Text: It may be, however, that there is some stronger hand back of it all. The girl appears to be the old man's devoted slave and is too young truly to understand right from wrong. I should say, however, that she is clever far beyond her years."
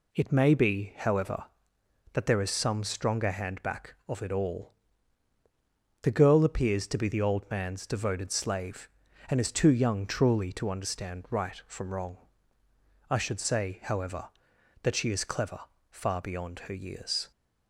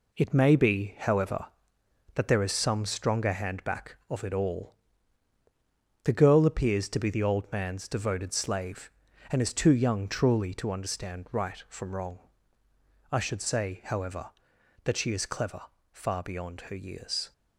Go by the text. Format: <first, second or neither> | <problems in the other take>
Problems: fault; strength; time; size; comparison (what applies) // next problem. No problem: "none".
first | gets quieter; throughout; 6 dB // pauses between "clever" and "far"; slight; at 15.6 s; 0.30 s long; slight in the first